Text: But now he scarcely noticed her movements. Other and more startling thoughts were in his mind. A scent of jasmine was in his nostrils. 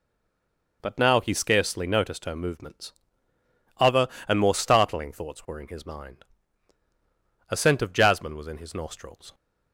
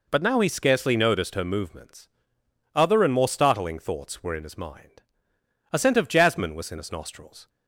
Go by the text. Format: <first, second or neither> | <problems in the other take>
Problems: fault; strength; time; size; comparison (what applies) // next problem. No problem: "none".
second | stays silent before the first word; slight; until 0.8 s; 0.8 s long